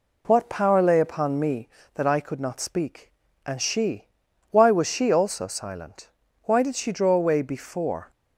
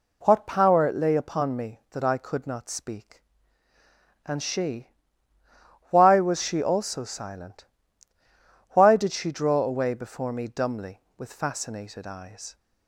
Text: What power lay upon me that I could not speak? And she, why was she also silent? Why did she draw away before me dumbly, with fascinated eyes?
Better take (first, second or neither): second